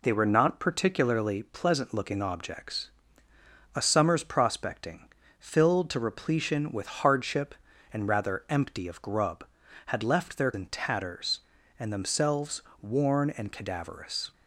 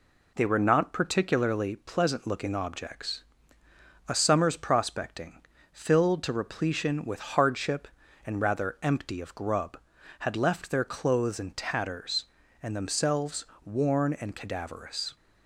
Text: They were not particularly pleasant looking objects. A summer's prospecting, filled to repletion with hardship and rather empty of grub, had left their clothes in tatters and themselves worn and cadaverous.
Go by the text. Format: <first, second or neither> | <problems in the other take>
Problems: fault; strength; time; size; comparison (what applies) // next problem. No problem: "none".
second | skips "clothes"; at 10.5 s // pauses between "themselves" and "worn"; slight; at 12.6 s; 0.22 s long; slight in the second